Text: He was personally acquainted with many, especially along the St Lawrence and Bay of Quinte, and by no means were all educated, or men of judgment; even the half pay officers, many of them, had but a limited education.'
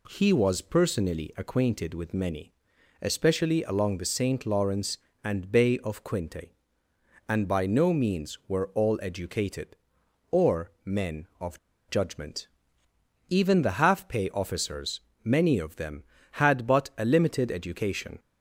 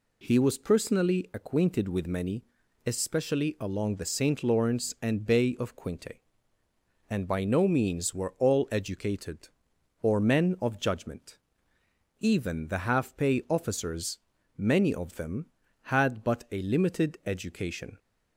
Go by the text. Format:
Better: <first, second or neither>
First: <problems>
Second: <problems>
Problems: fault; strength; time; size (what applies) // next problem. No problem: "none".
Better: second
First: pauses between "of" and "judgment"; slight; at 11.5 s; 0.29 s long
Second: none